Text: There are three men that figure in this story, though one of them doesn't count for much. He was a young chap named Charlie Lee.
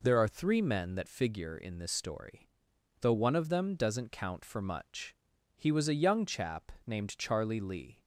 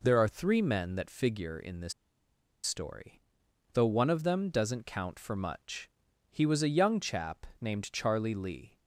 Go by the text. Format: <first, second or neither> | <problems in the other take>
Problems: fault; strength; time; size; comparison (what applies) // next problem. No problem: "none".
first | pauses between "this" and "story"; noticeable; at 1.9 s; 0.71 s long // pauses between "chap" and "named"; slight; at 7.4 s; 0.16 s long; slight in the first